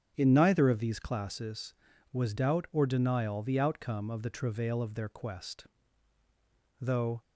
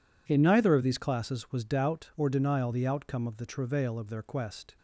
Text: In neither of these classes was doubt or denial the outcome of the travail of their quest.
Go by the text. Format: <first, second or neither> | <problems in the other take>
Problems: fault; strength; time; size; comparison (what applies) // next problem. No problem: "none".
second | starts louder than the rest; strong; until 1.1 s; 8 dB // goes on to say "Though"; slight; from 6.7 s on; 0.44 s long